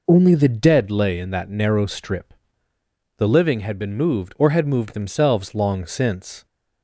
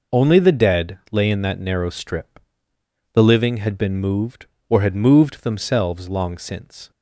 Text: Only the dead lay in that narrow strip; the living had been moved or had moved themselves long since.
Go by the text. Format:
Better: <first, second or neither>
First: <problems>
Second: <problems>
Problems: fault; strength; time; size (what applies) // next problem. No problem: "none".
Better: neither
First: none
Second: none